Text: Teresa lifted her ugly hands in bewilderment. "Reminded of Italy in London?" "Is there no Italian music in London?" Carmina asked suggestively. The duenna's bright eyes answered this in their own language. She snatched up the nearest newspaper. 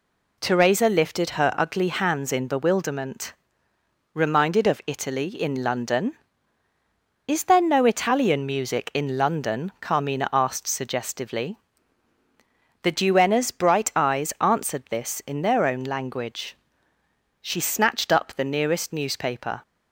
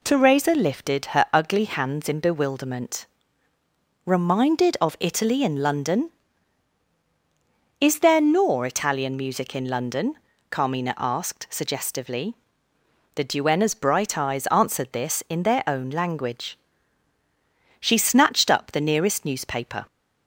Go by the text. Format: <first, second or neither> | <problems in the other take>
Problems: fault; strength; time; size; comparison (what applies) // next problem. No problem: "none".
first | says "nor" for "no"; at 8.2 s